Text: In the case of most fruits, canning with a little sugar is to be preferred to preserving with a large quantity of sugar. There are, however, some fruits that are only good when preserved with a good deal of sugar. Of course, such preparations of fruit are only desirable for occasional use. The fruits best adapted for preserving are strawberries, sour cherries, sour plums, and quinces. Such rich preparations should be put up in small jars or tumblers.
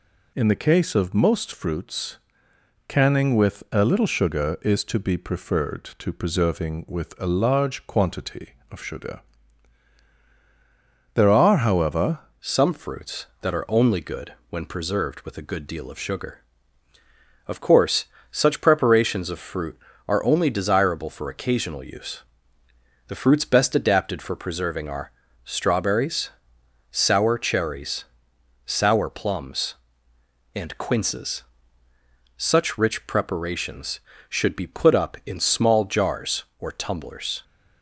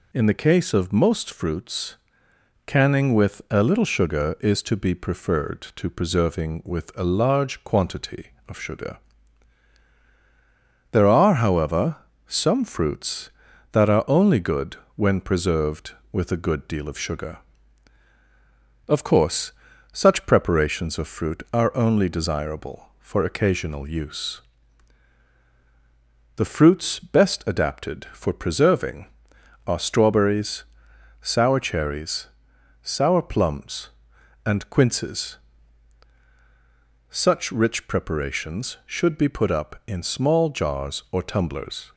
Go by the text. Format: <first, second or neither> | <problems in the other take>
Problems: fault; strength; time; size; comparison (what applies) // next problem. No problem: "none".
second | changes voice at "some"; from 12.4 s on; 25.0 s long // pauses between "good" and "when"; slight; at 14.3 s; 0.16 s long; slight in the second // pauses between "are" and "strawberries"; slight; at 25.1 s; 0.34 s long